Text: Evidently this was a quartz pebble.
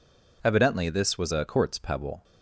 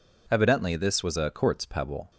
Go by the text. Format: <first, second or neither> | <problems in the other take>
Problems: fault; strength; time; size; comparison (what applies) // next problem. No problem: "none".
neither | none